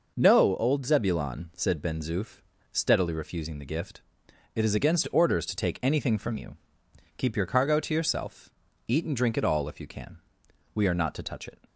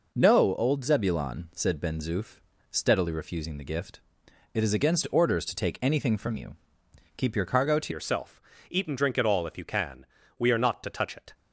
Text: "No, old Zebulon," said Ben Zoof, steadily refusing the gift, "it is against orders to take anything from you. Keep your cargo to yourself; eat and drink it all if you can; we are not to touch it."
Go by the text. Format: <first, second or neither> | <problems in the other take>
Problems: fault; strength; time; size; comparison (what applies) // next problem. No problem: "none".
first | changes voice at "yourself"; from 7.9 s on; 3.4 s long